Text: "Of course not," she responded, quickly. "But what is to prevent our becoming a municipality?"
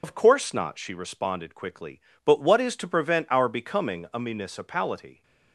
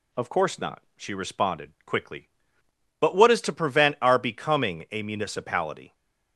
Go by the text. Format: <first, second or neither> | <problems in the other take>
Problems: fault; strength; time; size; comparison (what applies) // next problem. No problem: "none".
second | loses the start of "Of"; at 0.0 s; 70 ms